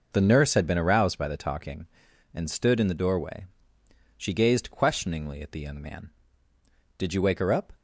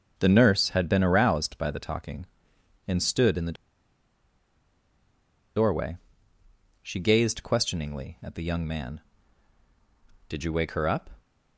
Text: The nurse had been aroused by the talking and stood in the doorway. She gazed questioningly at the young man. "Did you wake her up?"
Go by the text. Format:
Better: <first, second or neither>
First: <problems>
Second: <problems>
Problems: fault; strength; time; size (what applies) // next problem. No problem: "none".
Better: first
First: none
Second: starts louder than the rest; until 1.1 s; 6.5 dB // pauses between "the" and "doorway"; strong; at 3.5 s; 2.0 s long